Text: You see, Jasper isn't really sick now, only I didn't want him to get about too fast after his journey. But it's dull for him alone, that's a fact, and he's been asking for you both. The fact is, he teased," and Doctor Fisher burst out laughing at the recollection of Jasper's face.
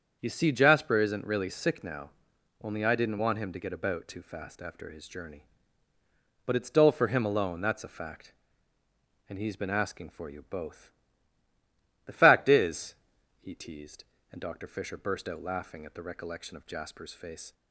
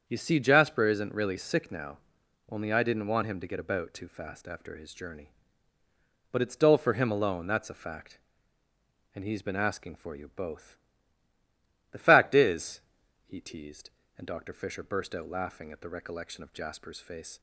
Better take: neither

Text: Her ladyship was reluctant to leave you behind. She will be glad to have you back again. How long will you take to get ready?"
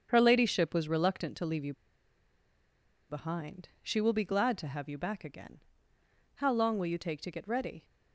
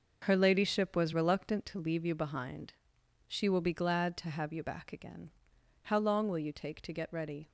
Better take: second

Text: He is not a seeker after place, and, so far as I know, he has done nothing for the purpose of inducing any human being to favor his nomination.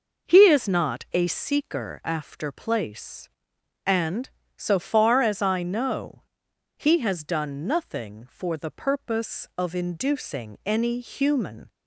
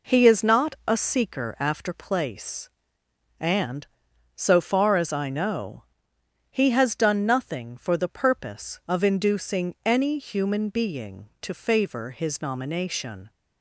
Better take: second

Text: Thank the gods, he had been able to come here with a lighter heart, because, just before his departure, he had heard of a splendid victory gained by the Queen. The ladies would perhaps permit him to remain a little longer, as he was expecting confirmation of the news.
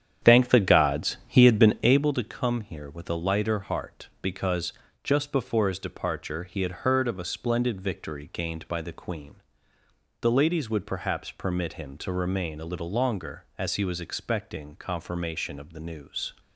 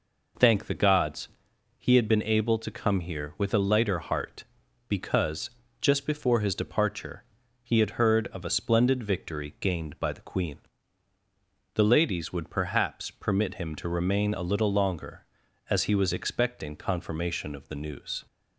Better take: second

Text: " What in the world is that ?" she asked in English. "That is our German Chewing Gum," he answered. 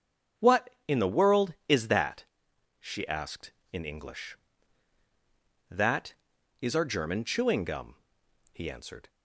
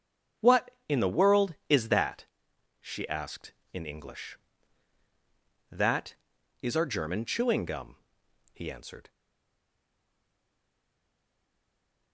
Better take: first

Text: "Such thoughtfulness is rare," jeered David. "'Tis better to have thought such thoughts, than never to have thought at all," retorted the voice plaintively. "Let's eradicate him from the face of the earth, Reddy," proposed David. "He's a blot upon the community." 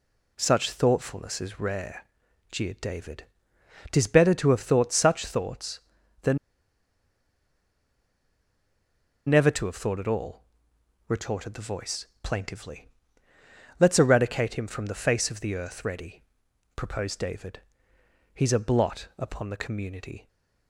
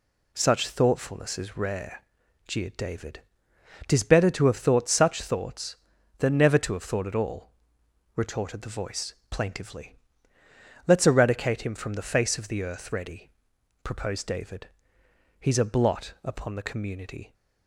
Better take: second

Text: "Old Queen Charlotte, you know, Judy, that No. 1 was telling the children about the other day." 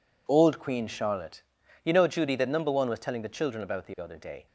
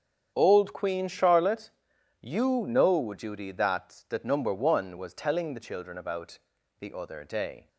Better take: first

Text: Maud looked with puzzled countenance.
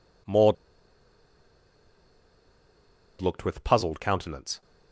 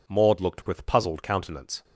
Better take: second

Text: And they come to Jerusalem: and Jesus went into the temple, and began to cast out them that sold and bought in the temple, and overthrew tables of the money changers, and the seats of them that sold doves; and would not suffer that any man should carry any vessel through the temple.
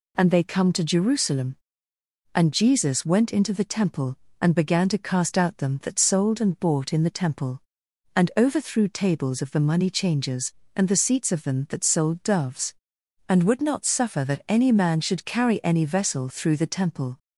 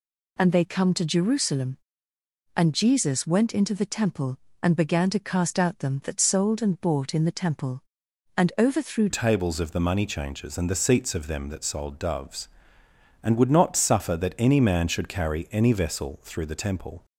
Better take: first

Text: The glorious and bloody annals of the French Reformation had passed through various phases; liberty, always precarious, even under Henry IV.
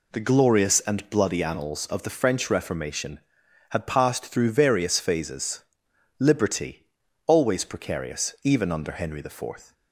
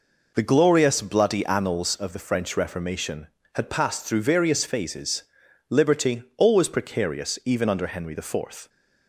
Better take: first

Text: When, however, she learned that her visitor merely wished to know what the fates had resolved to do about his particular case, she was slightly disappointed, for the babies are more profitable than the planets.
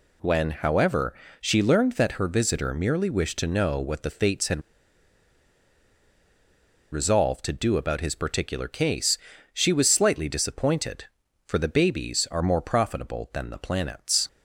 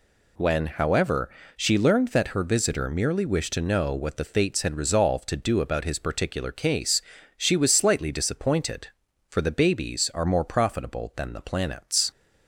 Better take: second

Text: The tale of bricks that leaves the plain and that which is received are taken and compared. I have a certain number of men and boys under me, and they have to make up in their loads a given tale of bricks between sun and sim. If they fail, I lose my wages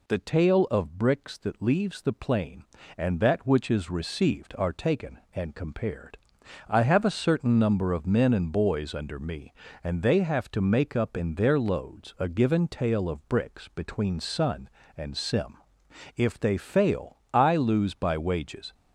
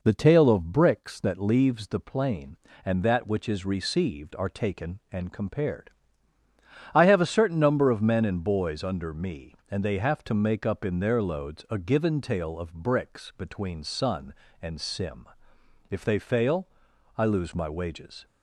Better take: second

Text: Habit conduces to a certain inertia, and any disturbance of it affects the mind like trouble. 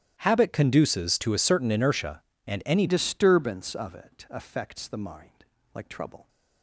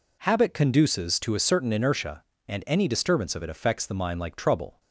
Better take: second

